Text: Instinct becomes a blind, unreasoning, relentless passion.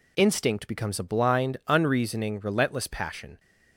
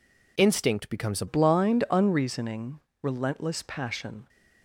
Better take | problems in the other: first | changes voice at "blind"; from 1.2 s on; 3.0 s long

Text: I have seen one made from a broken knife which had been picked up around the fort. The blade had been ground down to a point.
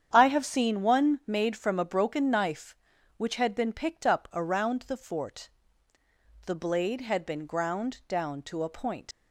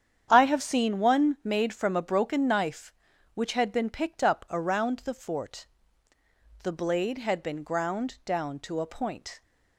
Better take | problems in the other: second | starts louder than the rest; strong; until 1.1 s; 8.5 dB; strong in the second // leaves "point" unfinished; at 9.1 s; 130 ms

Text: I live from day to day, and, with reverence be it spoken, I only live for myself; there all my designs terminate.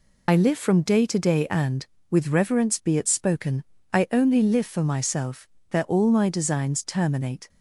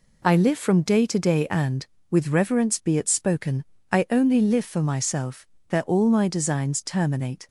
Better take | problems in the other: second | loses the start of "I"; at 0.2 s; 40 ms

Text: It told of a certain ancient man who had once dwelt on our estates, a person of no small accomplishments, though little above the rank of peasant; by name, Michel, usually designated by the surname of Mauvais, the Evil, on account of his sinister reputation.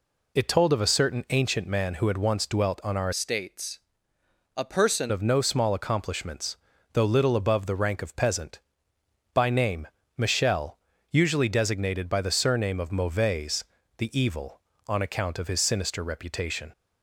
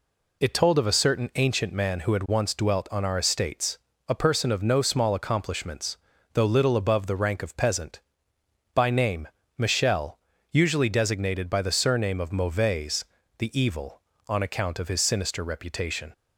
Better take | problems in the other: second | changes voice from "estates" to "person"; from 3.1 to 5.1 s; 2.0 s long

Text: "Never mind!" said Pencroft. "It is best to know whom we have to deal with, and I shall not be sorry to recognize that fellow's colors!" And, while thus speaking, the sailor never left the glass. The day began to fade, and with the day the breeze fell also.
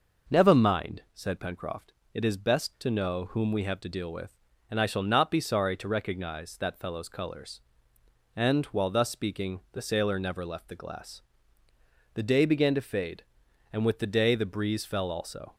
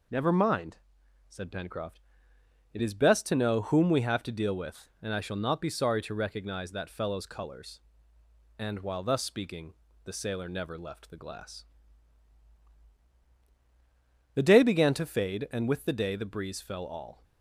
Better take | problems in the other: first | says "all" for "also"; at 16.8 s

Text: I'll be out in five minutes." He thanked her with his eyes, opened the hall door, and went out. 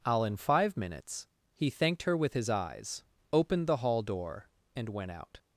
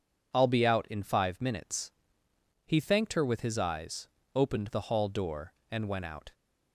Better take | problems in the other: second | skips "be out"; at 0.2 s

